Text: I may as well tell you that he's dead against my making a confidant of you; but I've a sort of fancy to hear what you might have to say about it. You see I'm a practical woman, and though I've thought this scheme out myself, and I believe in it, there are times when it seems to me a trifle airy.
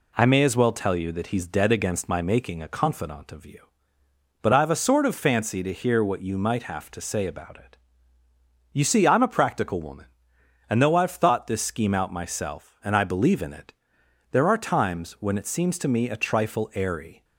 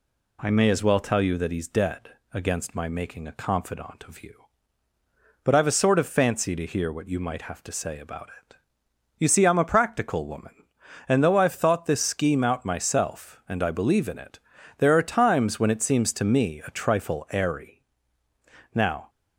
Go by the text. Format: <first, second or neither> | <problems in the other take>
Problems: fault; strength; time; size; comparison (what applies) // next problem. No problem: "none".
first | pauses between "dead" and "against"; slight; at 2.0 s; 0.24 s long // goes on to say "Now"; slight; from 18.7 s on; 0.36 s long